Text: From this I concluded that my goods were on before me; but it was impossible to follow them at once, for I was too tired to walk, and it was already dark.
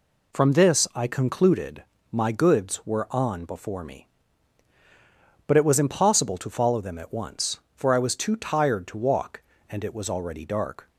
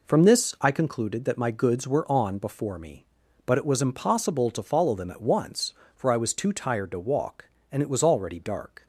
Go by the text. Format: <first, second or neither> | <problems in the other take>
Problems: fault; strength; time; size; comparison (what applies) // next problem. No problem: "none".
second | skips "that"; at 1.9 s